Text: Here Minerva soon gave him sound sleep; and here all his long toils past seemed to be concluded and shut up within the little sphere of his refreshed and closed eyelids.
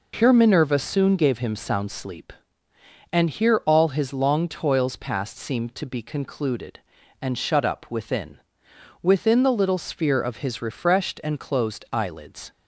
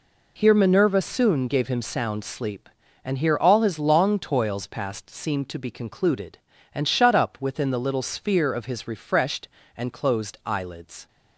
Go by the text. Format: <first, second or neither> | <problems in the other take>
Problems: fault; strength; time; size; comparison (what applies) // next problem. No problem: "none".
second | says "within" twice; at 9.0 s